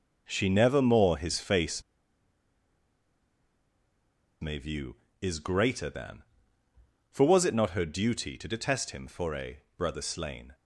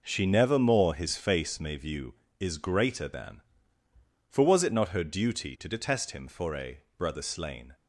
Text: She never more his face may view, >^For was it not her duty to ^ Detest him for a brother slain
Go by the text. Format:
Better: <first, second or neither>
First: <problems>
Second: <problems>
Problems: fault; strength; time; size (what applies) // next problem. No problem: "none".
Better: second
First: pauses between "face" and "may"; strong; at 1.8 s; 2.5 s long // pauses between "a" and "brother"; slight; at 9.6 s; 0.18 s long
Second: pauses between "a" and "brother"; slight; at 6.8 s; 0.18 s long